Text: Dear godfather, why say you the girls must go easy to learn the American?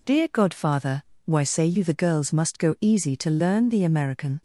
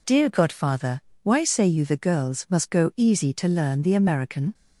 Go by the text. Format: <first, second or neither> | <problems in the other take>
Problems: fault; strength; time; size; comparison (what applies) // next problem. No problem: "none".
neither | none